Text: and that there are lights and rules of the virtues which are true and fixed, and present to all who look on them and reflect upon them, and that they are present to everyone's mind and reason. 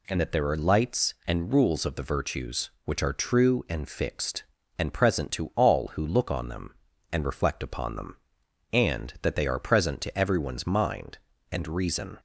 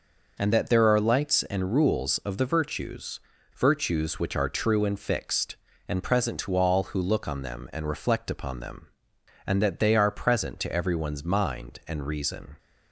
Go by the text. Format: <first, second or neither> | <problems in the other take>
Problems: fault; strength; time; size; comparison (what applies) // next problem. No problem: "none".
first | says "virtues" twice; at 3.5 s